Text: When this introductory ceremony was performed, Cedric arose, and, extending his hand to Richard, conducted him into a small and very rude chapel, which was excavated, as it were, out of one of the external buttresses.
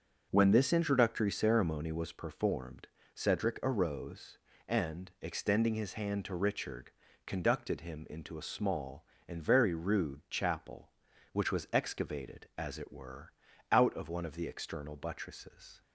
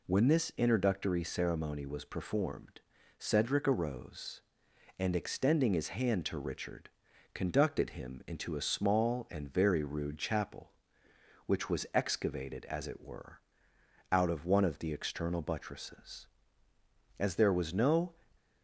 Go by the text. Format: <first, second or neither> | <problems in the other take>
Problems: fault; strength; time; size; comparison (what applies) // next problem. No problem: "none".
first | goes on to say "As there was no"; noticeable; from 17.1 s on; 0.96 s long